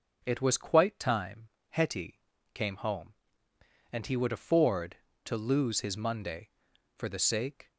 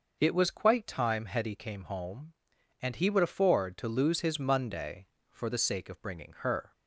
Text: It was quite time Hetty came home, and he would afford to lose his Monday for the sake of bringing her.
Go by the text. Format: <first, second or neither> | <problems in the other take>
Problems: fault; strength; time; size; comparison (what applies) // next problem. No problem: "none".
second | pauses between "time" and "Hetty"; slight; at 1.4 s; 0.22 s long // pauses between "Hetty" and "came"; slight; at 2.1 s; 0.34 s long // stops before "of bringing her"; at 7.6 s